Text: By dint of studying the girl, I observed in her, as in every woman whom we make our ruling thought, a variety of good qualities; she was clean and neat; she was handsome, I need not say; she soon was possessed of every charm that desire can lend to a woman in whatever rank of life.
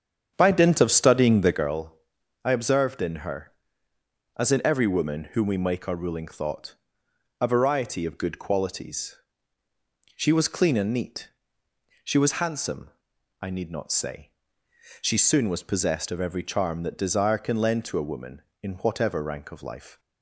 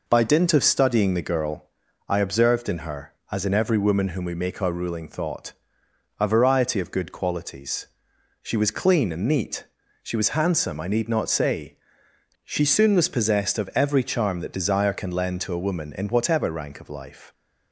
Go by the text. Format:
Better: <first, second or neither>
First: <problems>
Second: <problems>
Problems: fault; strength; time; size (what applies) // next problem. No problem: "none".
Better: second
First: starts louder than the rest; strong; until 1.7 s; 8 dB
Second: none